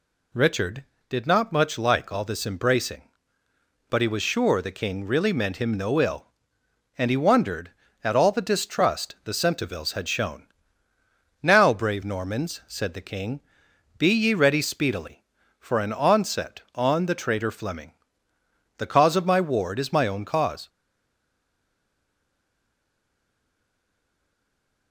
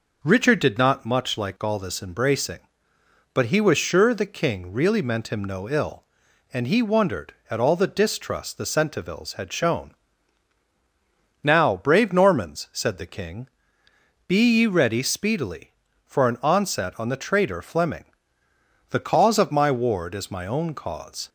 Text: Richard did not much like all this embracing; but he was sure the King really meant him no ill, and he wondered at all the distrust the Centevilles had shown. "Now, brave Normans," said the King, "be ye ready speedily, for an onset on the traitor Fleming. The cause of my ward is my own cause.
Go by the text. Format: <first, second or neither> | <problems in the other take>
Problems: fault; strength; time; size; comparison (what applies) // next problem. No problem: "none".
second | stays silent after the last word; strong; from 20.6 s on; 4.3 s long